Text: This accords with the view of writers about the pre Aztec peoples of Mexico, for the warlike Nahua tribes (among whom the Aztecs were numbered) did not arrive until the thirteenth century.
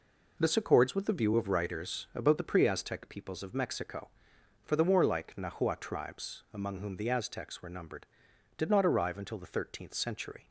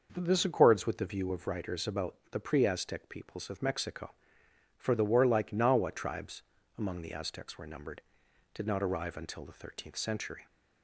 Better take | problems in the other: first | pauses between "about" and "the"; slight; at 2.1 s; 0.16 s long // skips "whom"; at 7.0 s

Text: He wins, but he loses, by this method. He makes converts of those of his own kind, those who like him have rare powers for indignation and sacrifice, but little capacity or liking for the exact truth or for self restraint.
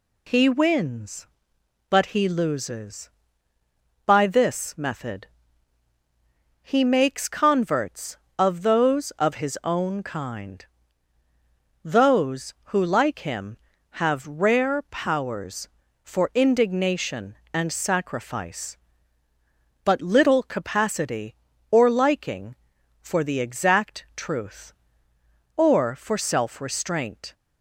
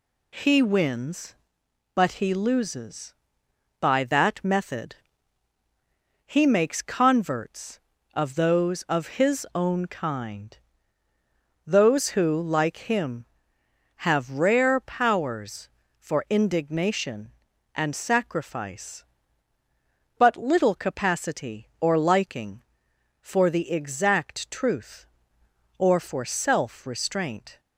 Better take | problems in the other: first | says "that" for "this"; at 4.0 s

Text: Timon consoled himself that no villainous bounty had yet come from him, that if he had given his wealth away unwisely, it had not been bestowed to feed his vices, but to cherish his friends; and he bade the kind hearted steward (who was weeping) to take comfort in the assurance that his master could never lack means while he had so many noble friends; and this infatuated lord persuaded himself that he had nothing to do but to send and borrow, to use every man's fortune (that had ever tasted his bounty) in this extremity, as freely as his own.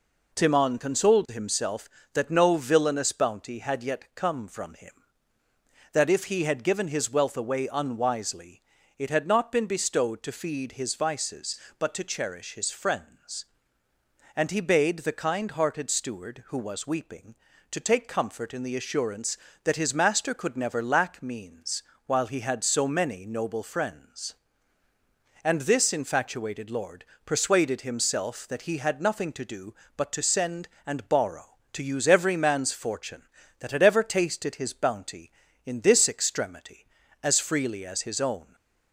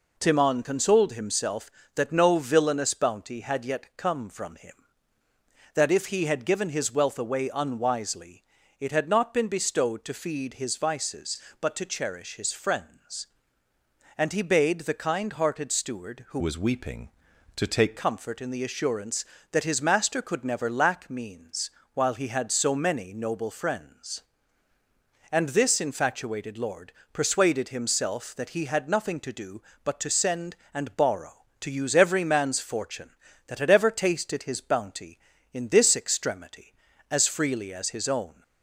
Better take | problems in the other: first | changes voice from "was" to "take"; from 16.3 to 17.9 s; 1.6 s long // pauses between "means" and "while"; slight; at 21.7 s; 0.24 s long; slight in the first // pauses between "lord" and "persuaded"; slight; at 26.9 s; 0.22 s long; slight in the first

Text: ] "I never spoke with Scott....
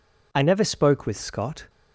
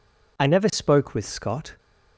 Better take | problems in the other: neither | none

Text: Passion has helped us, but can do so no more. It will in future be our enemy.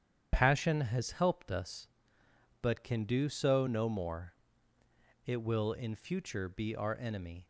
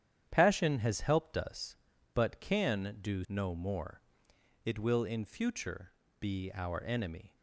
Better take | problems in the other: first | starts louder than the rest; strong; until 1.3 s; 10 dB; strong in the first // skips "so"; at 3.2 s // pauses between "future" and "be"; slight; at 5.9 s; 0.28 s long

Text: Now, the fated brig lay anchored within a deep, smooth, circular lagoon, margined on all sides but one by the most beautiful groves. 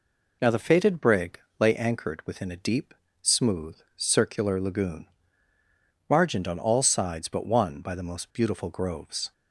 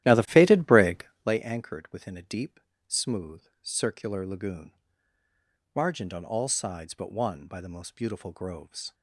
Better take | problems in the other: first | starts louder than the rest; strong; until 1.4 s; 13.5 dB // pauses between "brig" and "lay"; slight; at 1.0 s; 0.20 s long; slight in the first

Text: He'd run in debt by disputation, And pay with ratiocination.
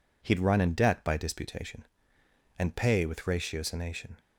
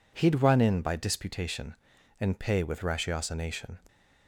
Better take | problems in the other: first | skips "debt"; at 0.8 s

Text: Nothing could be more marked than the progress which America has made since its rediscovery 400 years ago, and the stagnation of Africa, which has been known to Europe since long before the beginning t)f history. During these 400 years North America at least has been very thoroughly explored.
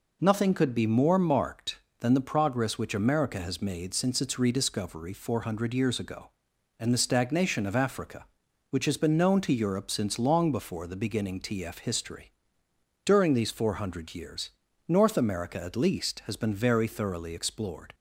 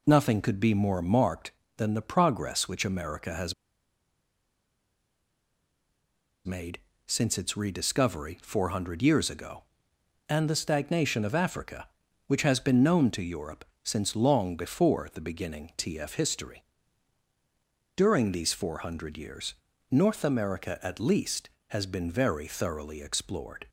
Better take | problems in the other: first | pauses between "has" and "made"; strong; at 3.5 s; 2.9 s long // pauses between "made" and "since"; slight; at 6.7 s; 0.28 s long // pauses between "Europe" and "since"; slight; at 13.6 s; 0.18 s long // pauses between "years" and "North"; slight; at 19.5 s; 0.36 s long; slight in the first

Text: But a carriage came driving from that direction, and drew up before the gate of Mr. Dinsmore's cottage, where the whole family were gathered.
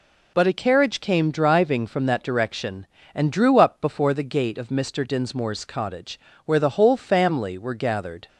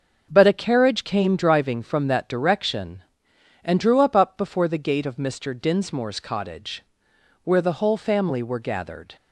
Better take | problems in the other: first | starts louder than the rest; until 1.3 s; 6 dB // says "up" twice; at 4.1 s

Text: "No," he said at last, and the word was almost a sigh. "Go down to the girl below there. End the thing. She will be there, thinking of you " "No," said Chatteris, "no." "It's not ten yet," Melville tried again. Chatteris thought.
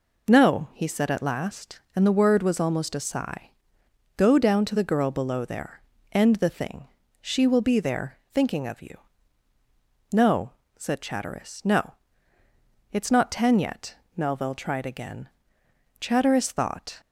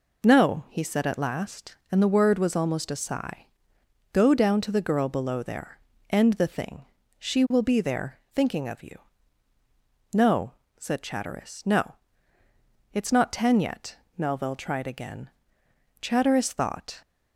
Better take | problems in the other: neither | none

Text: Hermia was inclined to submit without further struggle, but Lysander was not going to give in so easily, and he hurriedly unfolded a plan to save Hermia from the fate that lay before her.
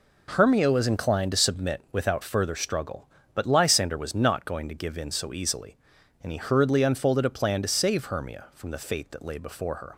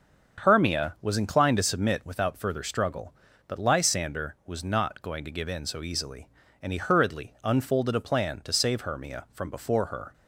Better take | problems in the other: first | starts louder than the rest; until 1.4 s; 6.5 dB // skips "the fate that lay"; at 9.4 s

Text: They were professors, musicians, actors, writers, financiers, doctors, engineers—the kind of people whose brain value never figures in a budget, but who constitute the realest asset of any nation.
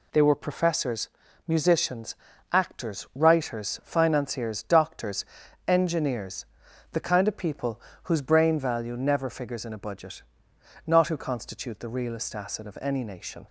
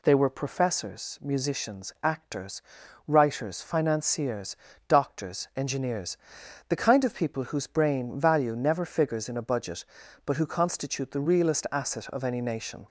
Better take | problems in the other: second | pauses between "people" and "whose"; slight; at 7.8 s; 0.24 s long // says "not" for "but"; at 10.8 s

